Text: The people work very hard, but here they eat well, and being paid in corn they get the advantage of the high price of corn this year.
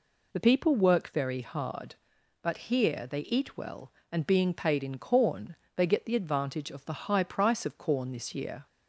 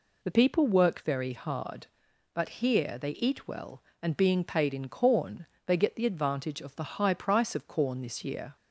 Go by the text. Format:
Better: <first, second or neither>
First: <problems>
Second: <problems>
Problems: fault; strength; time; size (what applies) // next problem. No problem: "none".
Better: neither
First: pauses between "corn" and "they"; slight; at 5.5 s; 0.18 s long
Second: pauses between "corn" and "they"; slight; at 5.4 s; 0.18 s long